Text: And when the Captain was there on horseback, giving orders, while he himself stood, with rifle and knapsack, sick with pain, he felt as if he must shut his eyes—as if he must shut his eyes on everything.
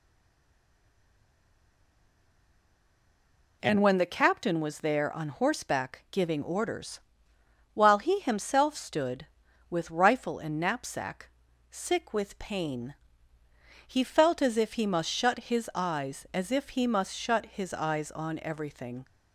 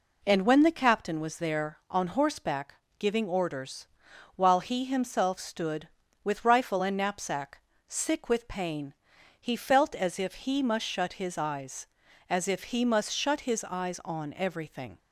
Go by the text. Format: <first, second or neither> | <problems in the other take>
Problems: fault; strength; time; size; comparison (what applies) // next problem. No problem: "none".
second | stays silent before the first word; strong; until 3.6 s; 3.6 s long